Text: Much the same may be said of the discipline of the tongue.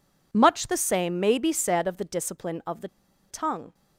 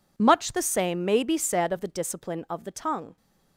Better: second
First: pauses between "the" and "tongue"; at 2.8 s; 0.42 s long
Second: none

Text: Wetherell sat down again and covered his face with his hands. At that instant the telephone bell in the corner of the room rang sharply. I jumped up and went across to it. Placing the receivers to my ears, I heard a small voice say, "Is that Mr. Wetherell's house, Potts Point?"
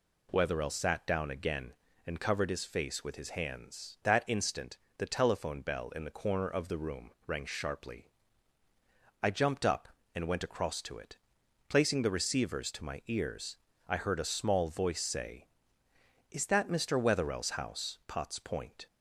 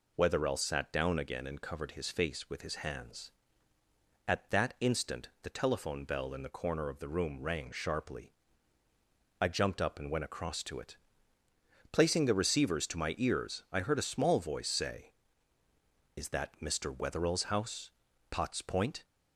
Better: second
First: skips "At"; at 4.0 s // pauses between "instant" and "the"; slight; at 4.7 s; 0.22 s long // pauses between "room" and "rang"; slight; at 7.1 s; 0.16 s long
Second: none

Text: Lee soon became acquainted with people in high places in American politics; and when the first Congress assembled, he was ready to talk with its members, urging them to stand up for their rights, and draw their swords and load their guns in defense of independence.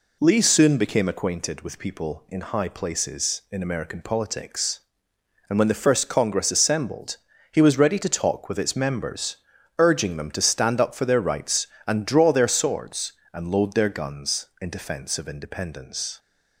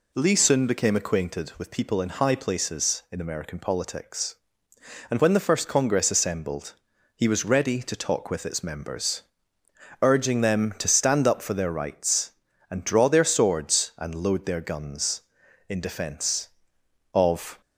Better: first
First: none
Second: stops before "independence"; at 17.6 s

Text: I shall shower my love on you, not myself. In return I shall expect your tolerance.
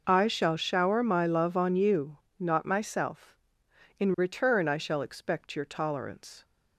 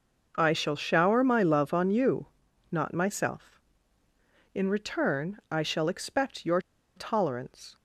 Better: first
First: none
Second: pauses between "your" and "tolerance"; at 6.5 s; 0.37 s long

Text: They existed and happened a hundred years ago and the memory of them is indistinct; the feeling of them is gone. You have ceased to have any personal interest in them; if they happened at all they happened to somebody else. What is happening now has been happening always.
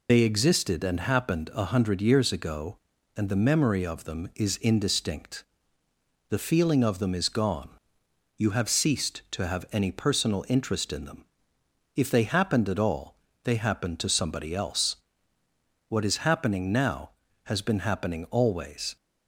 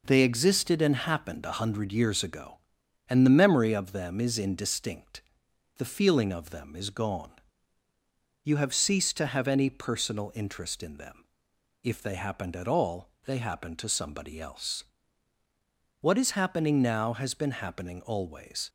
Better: second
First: loses the start of "They"; at 0.0 s; 70 ms // pauses between "all" and "they"; slight; at 13.1 s; 0.28 s long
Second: pauses between "all" and "they"; slight; at 13.0 s; 0.16 s long

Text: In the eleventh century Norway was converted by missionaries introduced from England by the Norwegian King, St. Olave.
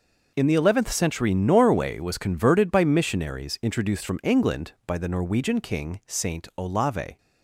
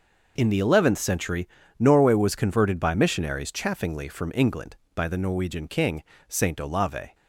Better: first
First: none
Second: pauses between "century" and "Norway"; slight; at 1.4 s; 0.32 s long // says "chaffingly" for "introduced"; at 3.5 s

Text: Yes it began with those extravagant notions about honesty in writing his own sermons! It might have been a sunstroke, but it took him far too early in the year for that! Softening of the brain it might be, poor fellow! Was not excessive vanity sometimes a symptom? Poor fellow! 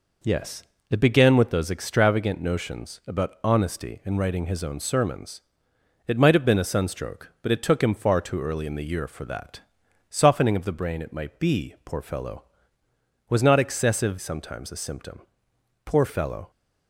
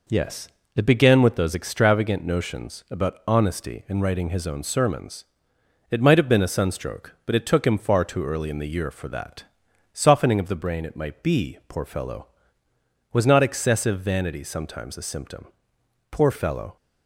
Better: second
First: pauses between "Yes" and "it"; slight; at 0.6 s; 0.28 s long // skips "vanity"; at 14.1 s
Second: pauses between "Yes" and "it"; slight; at 0.4 s; 0.28 s long

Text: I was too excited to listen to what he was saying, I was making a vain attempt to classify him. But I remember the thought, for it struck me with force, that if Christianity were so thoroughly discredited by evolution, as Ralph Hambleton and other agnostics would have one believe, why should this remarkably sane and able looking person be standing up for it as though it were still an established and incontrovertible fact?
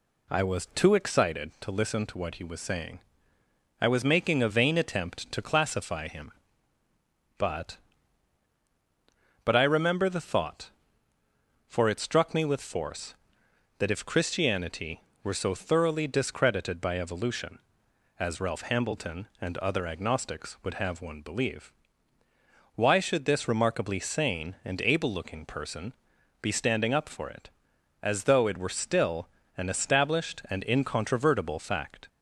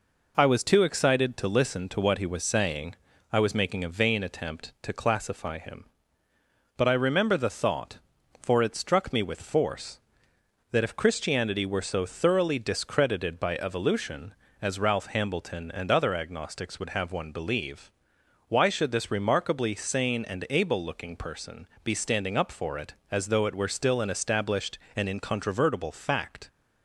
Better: second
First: says "But" twice; at 9.4 s // pauses between "person" and "be"; noticeable; at 25.9 s; 0.48 s long // pauses between "still" and "an"; slight; at 29.2 s; 0.30 s long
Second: pauses between "person" and "be"; slight; at 21.6 s; 0.18 s long

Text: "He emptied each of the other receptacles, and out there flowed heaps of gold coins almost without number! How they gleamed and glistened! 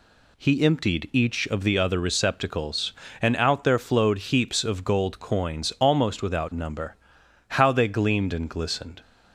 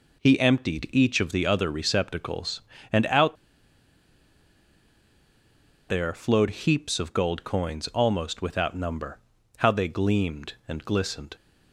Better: first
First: none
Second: pauses between "out" and "there"; strong; at 3.3 s; 2.5 s long

